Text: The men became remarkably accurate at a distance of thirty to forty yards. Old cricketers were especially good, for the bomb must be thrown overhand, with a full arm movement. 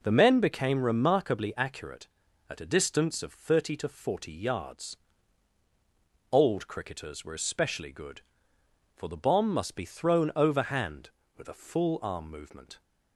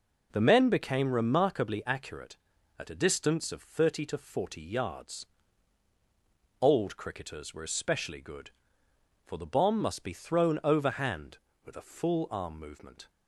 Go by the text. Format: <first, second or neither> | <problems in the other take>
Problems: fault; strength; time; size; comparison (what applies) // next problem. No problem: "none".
neither | none